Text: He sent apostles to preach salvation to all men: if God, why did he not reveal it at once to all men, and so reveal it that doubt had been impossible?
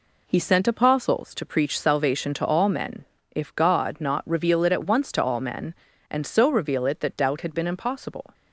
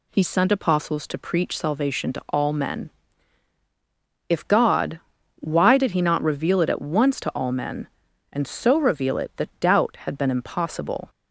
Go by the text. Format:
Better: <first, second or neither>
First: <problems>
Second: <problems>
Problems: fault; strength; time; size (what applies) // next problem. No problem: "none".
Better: second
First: skips "why did he"; at 4.0 s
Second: none